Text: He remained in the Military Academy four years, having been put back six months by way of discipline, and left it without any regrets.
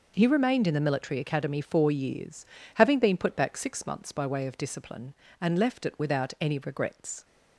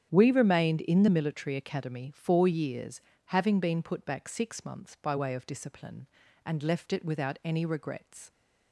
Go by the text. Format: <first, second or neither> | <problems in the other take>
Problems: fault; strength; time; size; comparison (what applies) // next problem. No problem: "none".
first | starts louder than the rest; strong; until 1.1 s; 9 dB // says "We" for "He"; at 0.1 s